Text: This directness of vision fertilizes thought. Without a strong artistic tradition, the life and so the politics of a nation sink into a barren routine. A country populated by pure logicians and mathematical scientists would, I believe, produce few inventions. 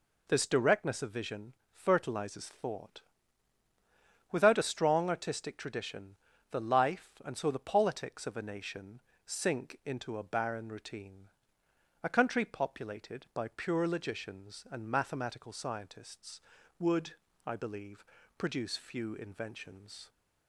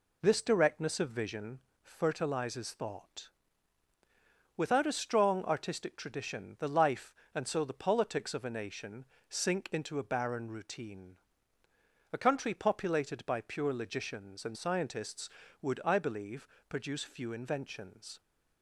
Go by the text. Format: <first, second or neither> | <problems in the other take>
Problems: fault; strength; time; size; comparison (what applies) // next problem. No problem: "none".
first | pauses between "vision" and "fertilizes"; slight; at 1.6 s; 0.22 s long; slight in the first // pauses between "nation" and "sink"; slight; at 9.0 s; 0.26 s long; slight in the first // skips "mathematical"; at 14.5 s